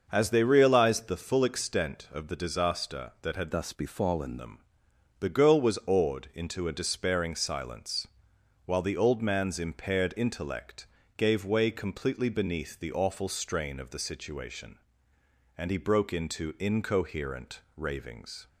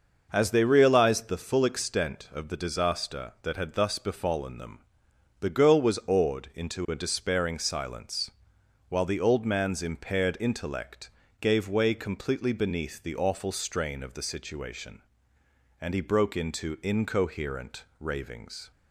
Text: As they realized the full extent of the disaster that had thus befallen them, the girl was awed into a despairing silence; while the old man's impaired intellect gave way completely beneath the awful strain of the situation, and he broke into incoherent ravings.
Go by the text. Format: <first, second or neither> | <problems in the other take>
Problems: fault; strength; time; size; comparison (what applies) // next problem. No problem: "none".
second | starts louder than the rest; until 1.1 s; 6 dB // changes voice from "thus" to "befallen"; from 3.5 to 4.3 s; 0.8 s long // pauses between "intellect" and "gave"; slight; at 10.8 s; 0.32 s long; slight in the second // pauses between "incoherent" and "ravings"; slight; at 17.5 s; 0.16 s long; slight in the second